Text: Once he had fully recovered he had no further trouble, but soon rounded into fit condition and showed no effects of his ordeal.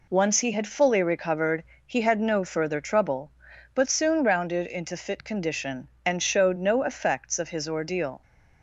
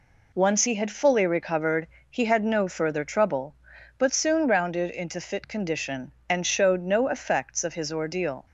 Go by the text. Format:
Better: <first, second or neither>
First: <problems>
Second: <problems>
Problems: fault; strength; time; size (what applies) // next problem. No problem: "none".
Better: neither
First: pauses between "recovered" and "he"; slight; at 1.6 s; 0.24 s long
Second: pauses between "recovered" and "he"; slight; at 1.8 s; 0.24 s long